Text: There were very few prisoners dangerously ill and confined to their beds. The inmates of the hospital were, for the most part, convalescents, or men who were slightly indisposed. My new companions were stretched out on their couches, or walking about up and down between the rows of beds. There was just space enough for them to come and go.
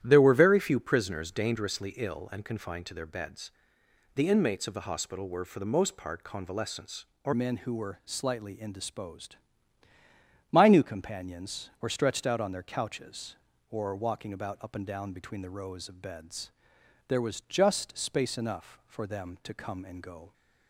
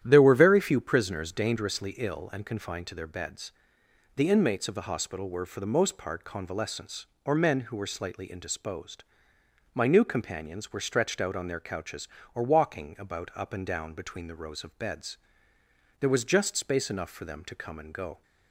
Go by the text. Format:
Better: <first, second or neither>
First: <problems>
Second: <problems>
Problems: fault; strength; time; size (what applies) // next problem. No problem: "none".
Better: second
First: starts louder than the rest; strong; until 1.0 s; 11.5 dB // changes voice at "men"; from 7.3 s on; 13.0 s long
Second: starts louder than the rest; strong; until 1.0 s; 11 dB